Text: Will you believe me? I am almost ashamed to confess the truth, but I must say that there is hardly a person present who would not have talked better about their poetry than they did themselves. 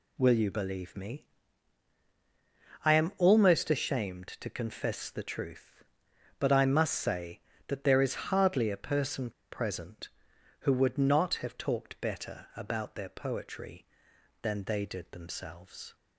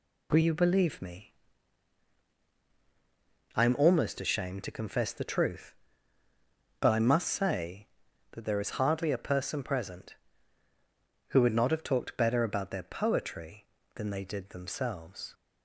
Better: second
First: pauses between "person" and "present"; slight; at 9.3 s; 0.20 s long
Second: none

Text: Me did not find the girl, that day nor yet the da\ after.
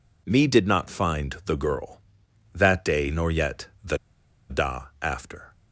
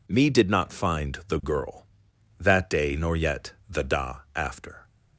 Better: second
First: pauses between "yet" and "the"; slight; at 3.6 s; 0.16 s long // pauses between "the" and "da"; noticeable; at 3.9 s; 0.52 s long // pauses between "da" and "after"; slight; at 4.8 s; 0.18 s long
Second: pauses between "yet" and "the"; slight; at 3.5 s; 0.16 s long // pauses between "da" and "after"; slight; at 4.1 s; 0.18 s long

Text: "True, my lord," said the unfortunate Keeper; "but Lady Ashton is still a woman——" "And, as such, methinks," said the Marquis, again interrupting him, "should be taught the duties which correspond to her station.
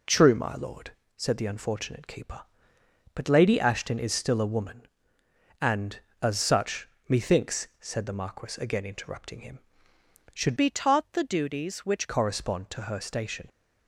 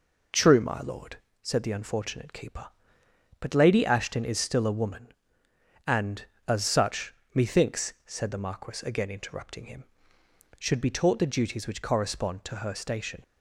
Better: second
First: changes voice from "be" to "which"; from 10.5 to 12.0 s; 1.5 s long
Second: none

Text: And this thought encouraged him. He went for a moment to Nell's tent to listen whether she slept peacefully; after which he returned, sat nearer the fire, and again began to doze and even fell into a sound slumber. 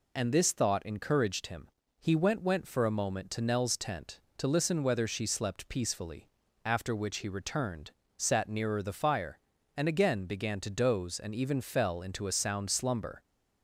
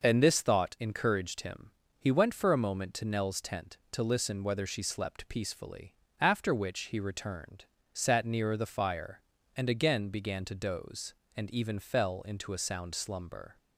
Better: second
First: says "went" twice; at 2.4 s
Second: none

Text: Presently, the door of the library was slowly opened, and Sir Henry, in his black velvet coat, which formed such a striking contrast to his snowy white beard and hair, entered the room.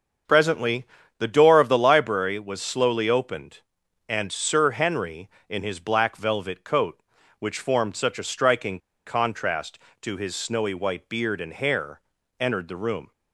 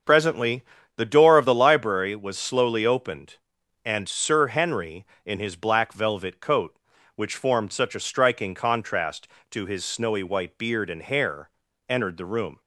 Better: second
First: starts louder than the rest; until 1.6 s; 6.5 dB // pauses between "striking" and "contrast"; slight; at 8.7 s; 0.27 s long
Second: starts louder than the rest; until 1.3 s; 7 dB

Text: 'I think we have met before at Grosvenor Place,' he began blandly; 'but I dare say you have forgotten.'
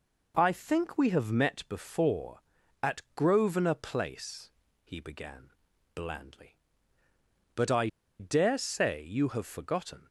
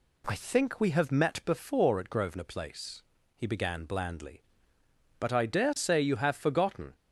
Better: second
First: pauses between "began" and "blandly"; at 5.5 s; 0.42 s long // pauses between "I" and "dare"; slight; at 7.8 s; 0.31 s long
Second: none

